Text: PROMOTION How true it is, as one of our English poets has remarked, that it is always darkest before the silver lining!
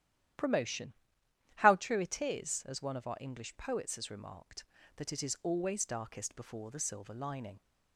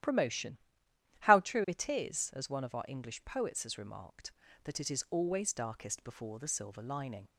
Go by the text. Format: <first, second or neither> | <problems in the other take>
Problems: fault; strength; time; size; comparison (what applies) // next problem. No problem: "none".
neither | starts louder than the rest; strong; the same in both // pauses between "PROMOTION" and "How"; noticeable; the same in both